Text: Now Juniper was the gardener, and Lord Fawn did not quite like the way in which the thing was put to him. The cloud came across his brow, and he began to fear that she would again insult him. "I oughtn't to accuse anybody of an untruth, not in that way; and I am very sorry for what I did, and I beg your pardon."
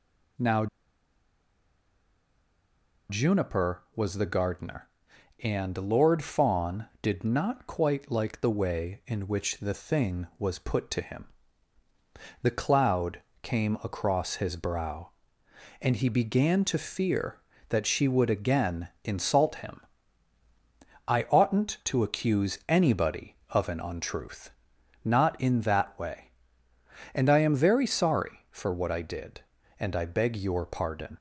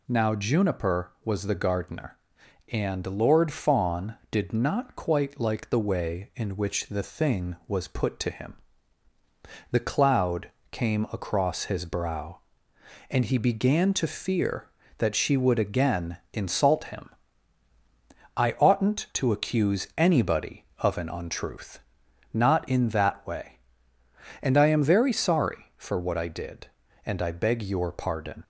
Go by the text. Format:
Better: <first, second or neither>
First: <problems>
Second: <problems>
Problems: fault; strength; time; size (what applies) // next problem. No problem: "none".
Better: second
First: pauses between "Now" and "Juniper"; strong; at 0.6 s; 2.4 s long // pauses between "cloud" and "came"; slight; at 13.2 s; 0.20 s long // pauses between "again" and "insult"; slight; at 18.8 s; 0.16 s long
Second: pauses between "cloud" and "came"; slight; at 10.4 s; 0.20 s long // pauses between "again" and "insult"; slight; at 16.1 s; 0.16 s long